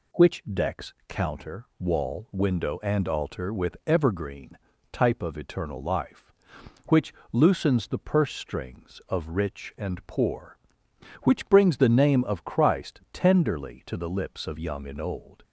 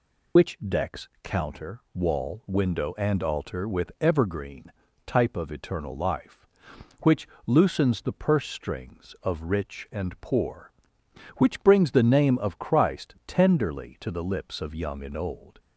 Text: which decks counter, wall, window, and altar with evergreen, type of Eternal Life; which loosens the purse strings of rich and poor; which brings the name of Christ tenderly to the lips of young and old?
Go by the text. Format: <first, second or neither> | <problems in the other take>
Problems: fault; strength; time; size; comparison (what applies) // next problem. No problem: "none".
first | loses the start of "which"; at 0.3 s; 70 ms // pauses between "which" and "loosens"; slight; at 7.2 s; 0.18 s long; slight in the first